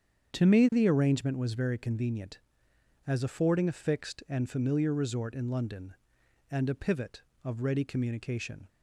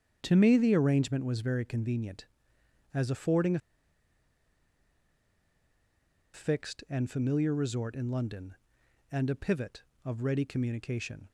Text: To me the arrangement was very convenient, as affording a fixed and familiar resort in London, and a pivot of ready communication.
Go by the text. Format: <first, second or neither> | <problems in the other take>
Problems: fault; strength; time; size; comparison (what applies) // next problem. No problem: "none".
first | starts louder than the rest; strong; until 1.2 s; 8 dB; strong in the first // pauses between "a" and "fixed"; strong; at 3.5 s; 2.7 s long